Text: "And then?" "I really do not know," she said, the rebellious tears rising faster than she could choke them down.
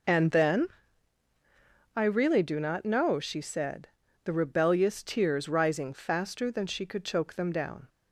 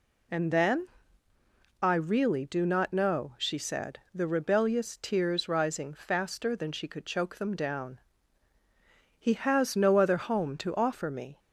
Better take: first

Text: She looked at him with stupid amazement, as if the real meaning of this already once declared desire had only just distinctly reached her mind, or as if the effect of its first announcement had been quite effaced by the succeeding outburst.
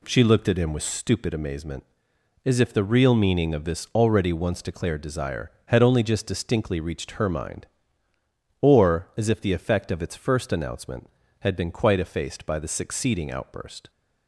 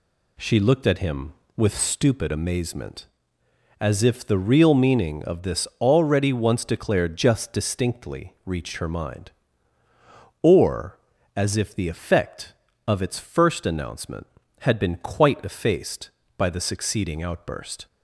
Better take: first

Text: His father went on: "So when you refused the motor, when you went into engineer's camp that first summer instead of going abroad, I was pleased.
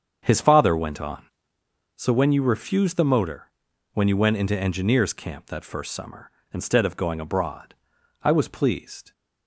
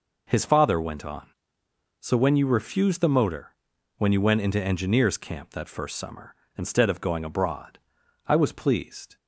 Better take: second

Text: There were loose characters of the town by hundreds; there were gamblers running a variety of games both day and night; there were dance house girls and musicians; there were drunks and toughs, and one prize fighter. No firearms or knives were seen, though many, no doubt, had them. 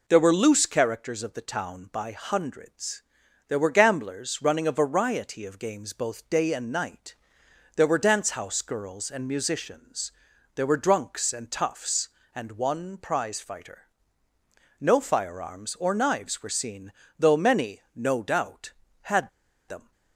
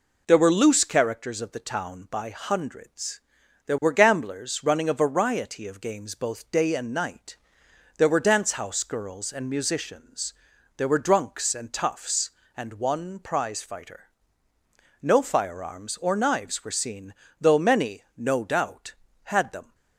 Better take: second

